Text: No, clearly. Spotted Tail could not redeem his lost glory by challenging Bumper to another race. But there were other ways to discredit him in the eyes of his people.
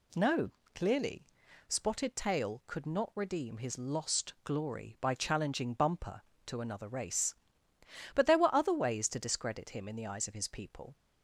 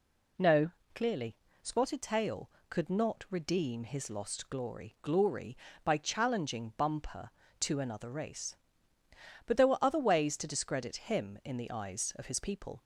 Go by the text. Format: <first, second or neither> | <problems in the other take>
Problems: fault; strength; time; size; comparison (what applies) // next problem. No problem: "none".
first | says "glory" twice; at 5.0 s